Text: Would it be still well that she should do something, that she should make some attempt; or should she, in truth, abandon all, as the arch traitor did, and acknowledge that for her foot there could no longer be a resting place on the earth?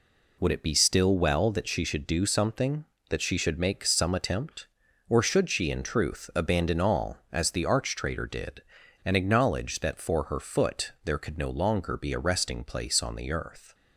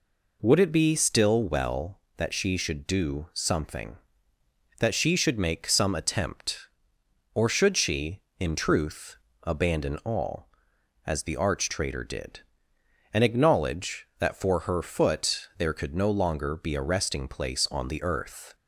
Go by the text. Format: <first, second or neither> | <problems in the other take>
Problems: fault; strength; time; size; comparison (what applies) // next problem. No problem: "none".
neither | none